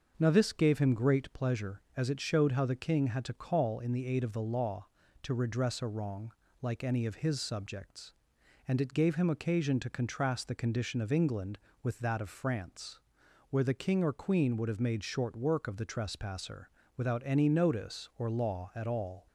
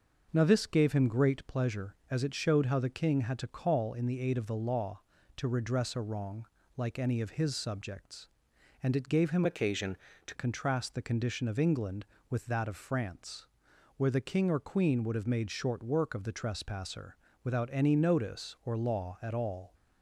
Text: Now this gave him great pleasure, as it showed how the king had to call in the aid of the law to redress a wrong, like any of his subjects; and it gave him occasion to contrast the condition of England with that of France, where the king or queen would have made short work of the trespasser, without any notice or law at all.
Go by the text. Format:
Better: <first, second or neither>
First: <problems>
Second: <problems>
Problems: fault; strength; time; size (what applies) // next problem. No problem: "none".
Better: first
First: starts louder than the rest; until 1.1 s; 6.5 dB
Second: starts louder than the rest; noticeable; until 1.3 s; 6 dB // changes voice from "occasion" to "to"; from 9.4 to 10.3 s; 0.9 s long